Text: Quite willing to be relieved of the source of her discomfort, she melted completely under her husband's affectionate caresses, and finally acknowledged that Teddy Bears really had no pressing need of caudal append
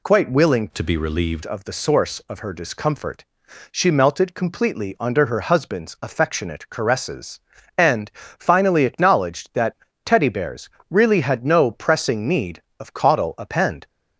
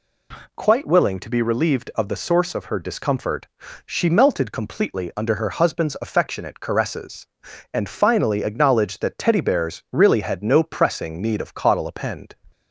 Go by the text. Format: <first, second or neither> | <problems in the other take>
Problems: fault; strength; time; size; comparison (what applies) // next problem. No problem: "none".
second | changes voice from "to" to "relieved"; from 0.7 to 1.4 s; 0.7 s long // pauses between "that" and "Teddy"; slight; at 9.7 s; 0.30 s long // pauses between "Bears" and "really"; slight; at 10.7 s; 0.18 s long